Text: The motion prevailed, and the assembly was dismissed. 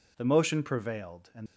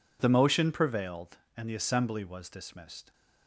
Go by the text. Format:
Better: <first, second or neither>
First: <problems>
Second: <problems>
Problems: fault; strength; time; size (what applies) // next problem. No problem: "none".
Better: second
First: stops before "the assembly was dismissed"; at 1.4 s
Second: none